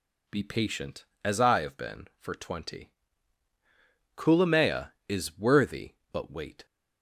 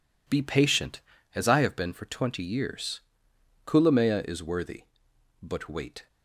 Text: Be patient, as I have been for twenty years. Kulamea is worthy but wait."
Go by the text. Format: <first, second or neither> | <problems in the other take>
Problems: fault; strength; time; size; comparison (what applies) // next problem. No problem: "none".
second | skips "years"; at 3.5 s